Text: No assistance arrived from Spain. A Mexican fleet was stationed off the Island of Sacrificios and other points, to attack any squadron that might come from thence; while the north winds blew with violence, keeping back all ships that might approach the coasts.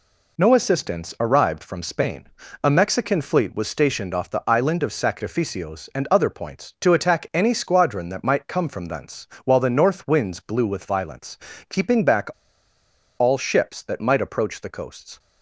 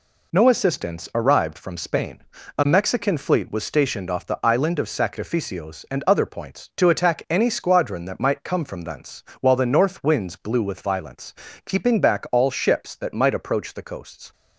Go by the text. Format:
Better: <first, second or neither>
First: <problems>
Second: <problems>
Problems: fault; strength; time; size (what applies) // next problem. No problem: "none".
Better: second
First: pauses between "back" and "all"; noticeable; at 12.2 s; 0.89 s long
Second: none